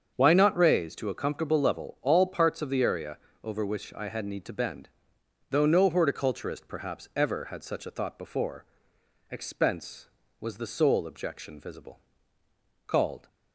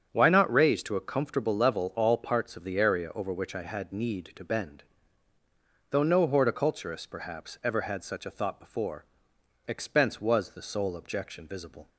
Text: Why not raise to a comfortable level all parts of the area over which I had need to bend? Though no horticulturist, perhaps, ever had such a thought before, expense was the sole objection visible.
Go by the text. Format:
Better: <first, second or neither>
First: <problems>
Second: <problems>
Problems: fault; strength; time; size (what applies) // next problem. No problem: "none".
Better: second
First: starts louder than the rest; until 1.1 s; 7 dB // pauses between "area" and "over"; slight; at 3.1 s; 0.26 s long // goes on to say "Called"; slight; from 12.8 s on; 0.42 s long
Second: starts louder than the rest; strong; until 1.1 s; 7.5 dB